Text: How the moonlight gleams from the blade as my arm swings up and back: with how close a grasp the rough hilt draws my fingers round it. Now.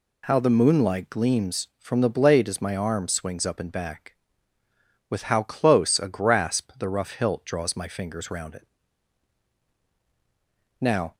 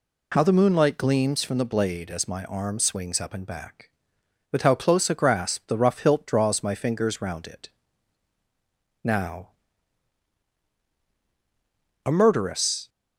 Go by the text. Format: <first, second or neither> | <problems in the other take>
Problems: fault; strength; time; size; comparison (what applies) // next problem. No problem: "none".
first | goes on to say "A murderess"; noticeable; from 12.0 s on; 0.82 s long